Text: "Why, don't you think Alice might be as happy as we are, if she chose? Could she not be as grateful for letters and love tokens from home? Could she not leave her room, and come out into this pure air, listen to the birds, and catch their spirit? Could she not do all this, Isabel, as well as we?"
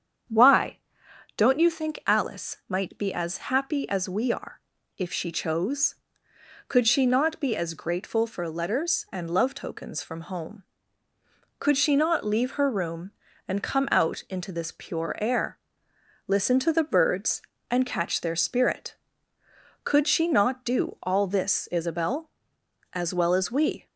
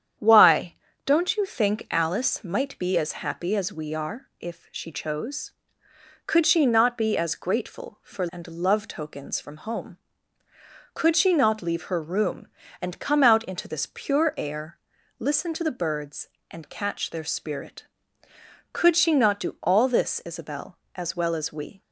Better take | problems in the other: first | starts louder than the rest; strong; until 1.4 s; 9 dB; strong in the first // skips "letters"; at 8.2 s

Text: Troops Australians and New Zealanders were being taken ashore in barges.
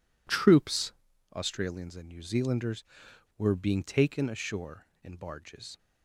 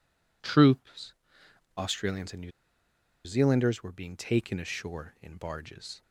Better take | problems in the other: first | pauses between "Troops" and "Australians"; noticeable; at 1.1 s; 0.64 s long; also in the first // pauses between "New" and "Zealanders"; noticeable; at 2.5 s; 0.74 s long

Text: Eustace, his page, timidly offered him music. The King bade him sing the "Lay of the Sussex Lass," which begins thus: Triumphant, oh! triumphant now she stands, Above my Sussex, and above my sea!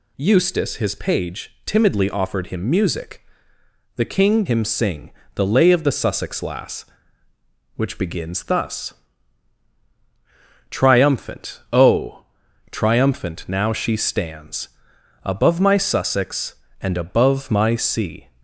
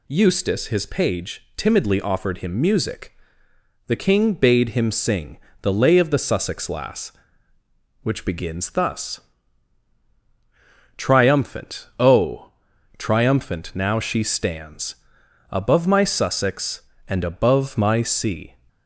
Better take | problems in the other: second | skips "bade"; at 4.4 s // pauses between "sing" and "the"; slight; at 5.1 s; 0.24 s long; slight in the second

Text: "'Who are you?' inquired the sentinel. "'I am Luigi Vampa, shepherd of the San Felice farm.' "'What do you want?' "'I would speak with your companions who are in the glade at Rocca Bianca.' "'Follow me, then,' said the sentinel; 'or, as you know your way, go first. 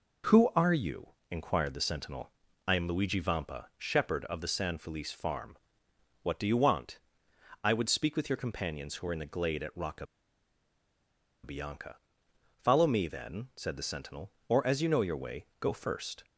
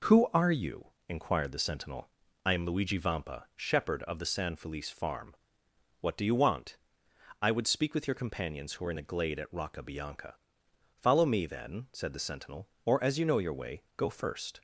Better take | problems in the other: second | pauses between "Rocca" and "Bianca"; strong; at 10.0 s; 1.3 s long

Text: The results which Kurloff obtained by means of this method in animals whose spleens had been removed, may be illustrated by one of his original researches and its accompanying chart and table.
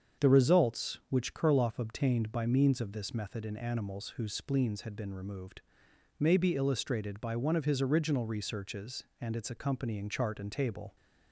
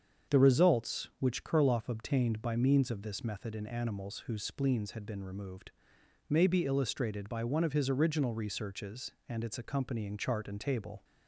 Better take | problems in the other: neither | starts louder than the rest; strong; the same in both

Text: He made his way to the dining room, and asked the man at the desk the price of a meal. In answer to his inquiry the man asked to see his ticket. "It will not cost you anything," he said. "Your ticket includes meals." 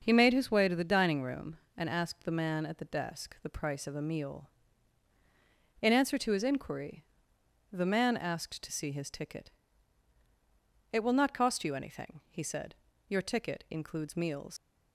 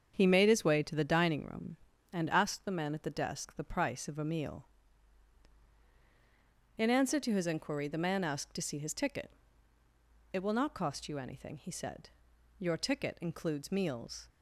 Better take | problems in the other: second | starts louder than the rest; until 1.0 s; 6.5 dB; strong in the second // pauses between "inquiry" and "the"; noticeable; at 7.0 s; 0.66 s long // leaves "meals" unfinished; at 14.5 s; 100 ms

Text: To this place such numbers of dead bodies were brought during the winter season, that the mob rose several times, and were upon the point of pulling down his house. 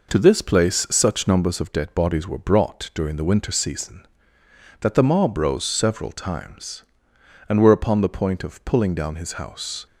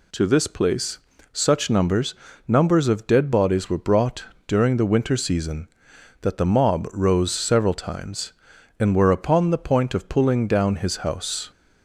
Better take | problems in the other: first | pauses between "place" and "such"; slight; at 0.9 s; 0.34 s long // says "numbers" twice; at 2.4 s // pauses between "brought" and "during"; slight; at 4.2 s; 0.22 s long

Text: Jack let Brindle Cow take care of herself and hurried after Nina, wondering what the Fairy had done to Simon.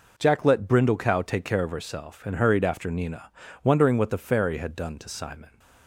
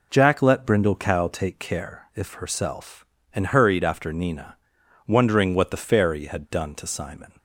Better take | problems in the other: first | says "if" for "of"; at 2.1 s

